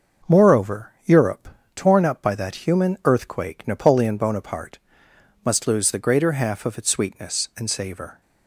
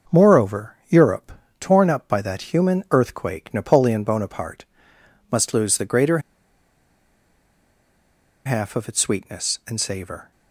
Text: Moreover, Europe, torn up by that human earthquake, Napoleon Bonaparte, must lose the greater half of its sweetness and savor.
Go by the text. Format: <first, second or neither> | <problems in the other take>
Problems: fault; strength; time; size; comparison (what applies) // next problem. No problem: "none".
first | starts louder than the rest; noticeable; until 1.2 s; 6 dB; noticeable in the first // pauses between "greater" and "half"; strong; at 6.1 s; 2.2 s long